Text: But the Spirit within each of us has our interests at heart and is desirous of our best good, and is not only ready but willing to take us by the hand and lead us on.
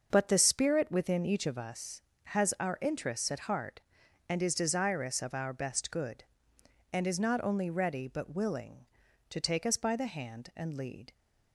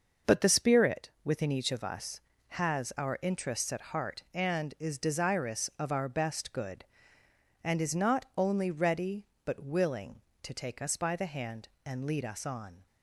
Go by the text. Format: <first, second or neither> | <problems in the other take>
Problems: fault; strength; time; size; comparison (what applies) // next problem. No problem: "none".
second | starts louder than the rest; until 1.1 s; 6.5 dB; noticeable in the second // stops before "us on"; at 11.1 s